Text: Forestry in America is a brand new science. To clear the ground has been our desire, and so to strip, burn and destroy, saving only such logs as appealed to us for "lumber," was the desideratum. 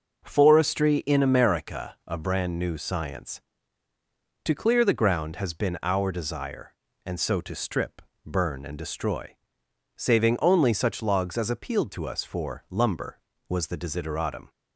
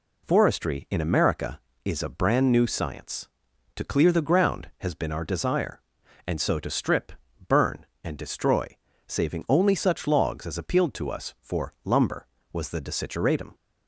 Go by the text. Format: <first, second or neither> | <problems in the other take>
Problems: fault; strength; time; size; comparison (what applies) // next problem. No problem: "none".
second | skips "is"; at 2.0 s